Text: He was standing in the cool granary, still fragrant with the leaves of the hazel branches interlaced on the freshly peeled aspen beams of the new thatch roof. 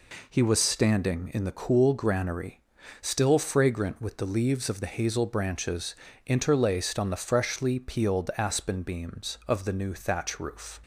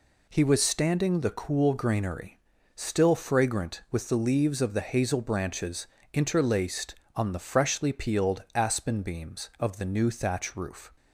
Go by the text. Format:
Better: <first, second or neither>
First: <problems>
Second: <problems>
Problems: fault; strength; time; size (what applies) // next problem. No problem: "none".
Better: first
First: pauses between "branches" and "interlaced"; slight; at 5.9 s; 0.30 s long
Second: skips "in"; at 1.2 s // pauses between "branches" and "interlaced"; slight; at 5.8 s; 0.26 s long